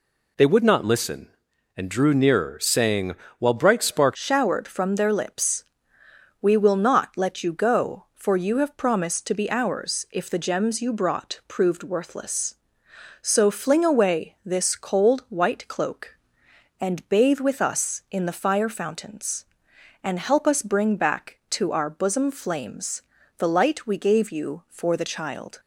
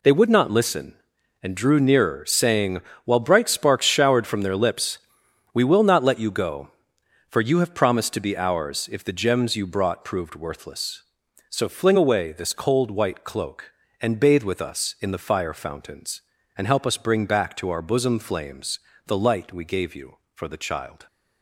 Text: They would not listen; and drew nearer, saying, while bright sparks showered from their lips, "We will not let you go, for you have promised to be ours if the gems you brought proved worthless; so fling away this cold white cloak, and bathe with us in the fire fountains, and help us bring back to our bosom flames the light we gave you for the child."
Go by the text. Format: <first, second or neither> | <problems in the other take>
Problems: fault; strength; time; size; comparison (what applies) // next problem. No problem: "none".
second | changes voice at "showered"; from 4.1 s on; 21.4 s long // pauses between "flames" and "the"; at 23.0 s; 0.38 s long; slight in the second